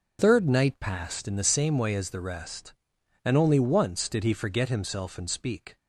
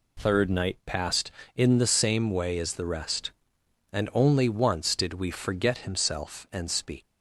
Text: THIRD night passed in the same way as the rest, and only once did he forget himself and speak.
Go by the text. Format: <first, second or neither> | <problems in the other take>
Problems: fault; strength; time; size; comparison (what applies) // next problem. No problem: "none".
first | says "we" for "he"; at 5.1 s